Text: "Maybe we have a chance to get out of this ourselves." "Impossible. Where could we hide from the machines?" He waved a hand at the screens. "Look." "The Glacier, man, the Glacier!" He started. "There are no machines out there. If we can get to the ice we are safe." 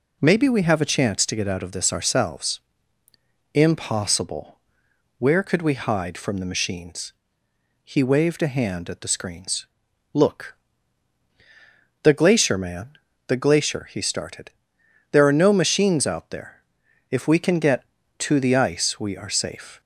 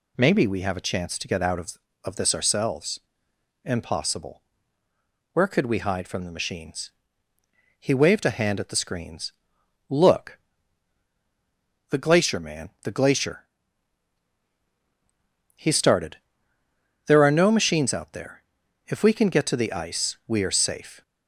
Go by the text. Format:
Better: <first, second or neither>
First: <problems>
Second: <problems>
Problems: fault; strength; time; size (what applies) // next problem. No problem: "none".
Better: first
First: none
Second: says "of" twice; at 2.0 s